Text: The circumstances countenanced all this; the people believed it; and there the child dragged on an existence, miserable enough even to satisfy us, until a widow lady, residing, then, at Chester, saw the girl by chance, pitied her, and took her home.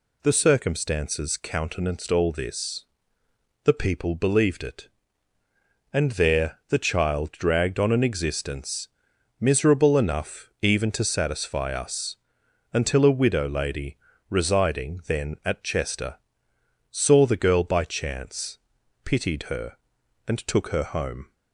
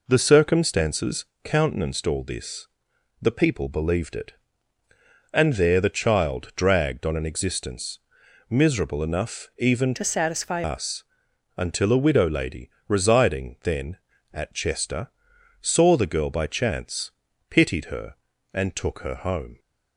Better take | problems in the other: first | pauses between "circumstances" and "countenanced"; slight; at 1.2 s; 0.18 s long // changes voice from "to" to "satisfy"; from 9.9 to 10.6 s; 0.7 s long

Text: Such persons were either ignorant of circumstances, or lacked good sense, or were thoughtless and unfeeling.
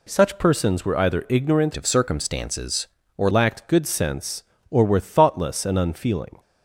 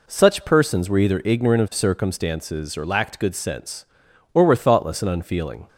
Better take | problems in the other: second | changes voice from "of" to "or"; from 1.7 to 3.2 s; 1.5 s long

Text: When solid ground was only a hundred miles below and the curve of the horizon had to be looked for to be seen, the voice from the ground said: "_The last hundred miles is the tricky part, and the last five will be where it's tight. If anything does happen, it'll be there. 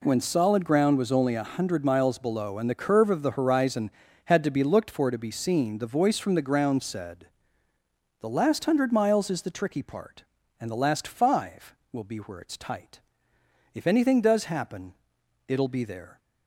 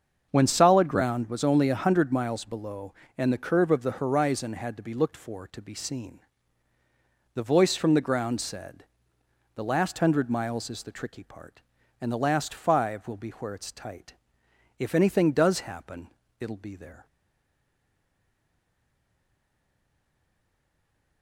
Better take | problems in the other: first | starts louder than the rest; until 1.3 s; 7 dB // stays silent after the last word; strong; from 17.0 s on; 4.2 s long

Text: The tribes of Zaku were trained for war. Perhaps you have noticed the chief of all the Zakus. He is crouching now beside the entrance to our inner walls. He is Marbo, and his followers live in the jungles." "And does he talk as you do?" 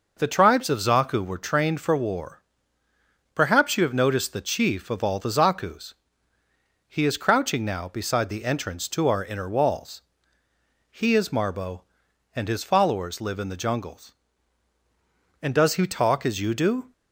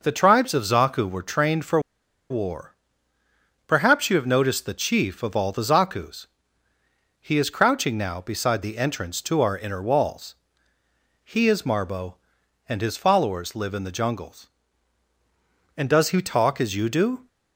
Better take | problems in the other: first | pauses between "for" and "war"; noticeable; at 1.7 s; 0.51 s long

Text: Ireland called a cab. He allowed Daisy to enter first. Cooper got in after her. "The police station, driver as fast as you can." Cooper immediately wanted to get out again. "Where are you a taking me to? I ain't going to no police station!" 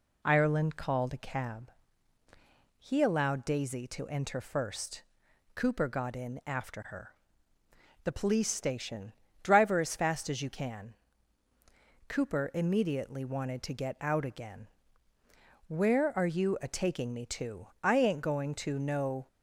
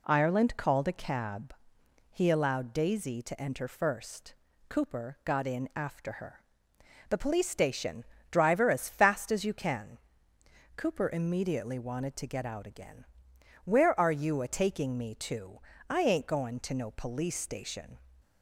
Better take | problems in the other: second | stops before "police station"; at 19.2 s

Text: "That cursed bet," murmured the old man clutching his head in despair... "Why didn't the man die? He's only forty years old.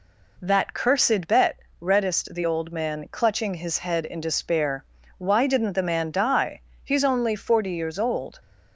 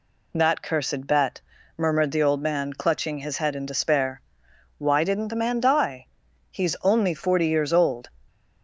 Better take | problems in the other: second | says "reddest" for "murmured"; at 1.7 s

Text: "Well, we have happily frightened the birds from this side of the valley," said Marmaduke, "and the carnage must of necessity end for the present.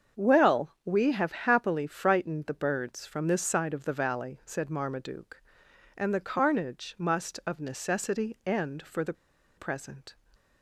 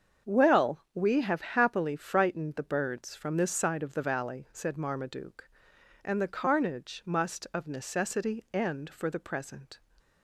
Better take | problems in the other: second | starts louder than the rest; until 1.2 s; 7 dB; also in the second // pauses between "the" and "present"; at 9.1 s; 0.44 s long

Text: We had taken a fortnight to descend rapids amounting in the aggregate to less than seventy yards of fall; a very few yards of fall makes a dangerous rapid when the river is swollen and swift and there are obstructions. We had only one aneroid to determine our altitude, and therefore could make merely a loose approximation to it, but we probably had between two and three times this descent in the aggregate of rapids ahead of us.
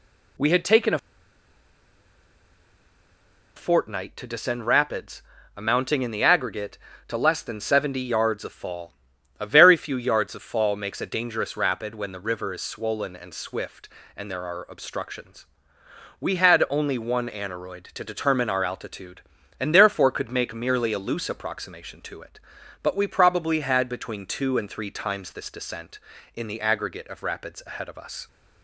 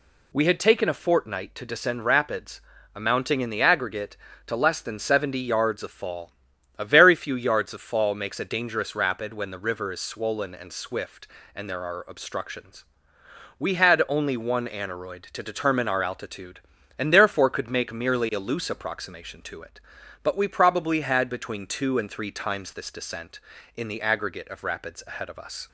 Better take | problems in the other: second | pauses between "a" and "fortnight"; strong; at 0.9 s; 2.5 s long // pauses between "rapids" and "amounting"; slight; at 5.2 s; 0.34 s long; slight in the second

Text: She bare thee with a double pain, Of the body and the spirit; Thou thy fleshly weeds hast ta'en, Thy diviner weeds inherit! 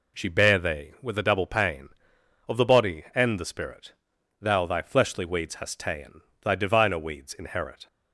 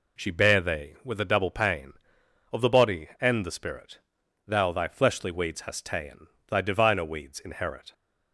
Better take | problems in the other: neither | none

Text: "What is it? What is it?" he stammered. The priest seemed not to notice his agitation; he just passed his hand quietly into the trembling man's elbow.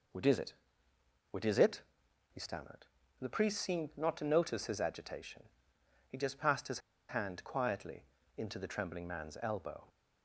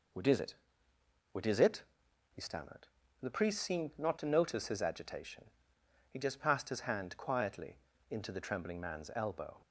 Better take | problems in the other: second | pauses between "his" and "hand"; slight; at 6.7 s; 0.28 s long // pauses between "quietly" and "into"; slight; at 8.0 s; 0.32 s long; slight in the second

